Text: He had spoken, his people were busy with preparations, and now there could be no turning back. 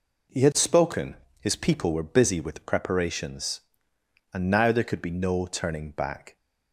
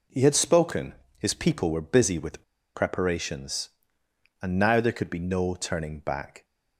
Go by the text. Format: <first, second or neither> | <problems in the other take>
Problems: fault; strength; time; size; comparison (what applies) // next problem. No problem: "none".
first | pauses between "with" and "preparations"; slight; at 2.4 s; 0.32 s long